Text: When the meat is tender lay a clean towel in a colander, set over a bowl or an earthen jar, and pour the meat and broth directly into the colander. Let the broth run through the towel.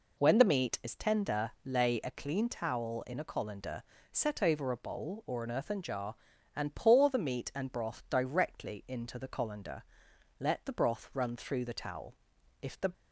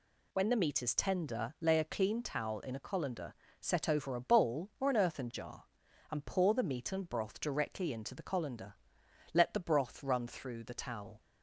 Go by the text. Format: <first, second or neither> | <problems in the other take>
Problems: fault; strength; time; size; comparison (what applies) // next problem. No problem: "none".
second | goes on to say "If the"; slight; from 12.6 s on; 0.30 s long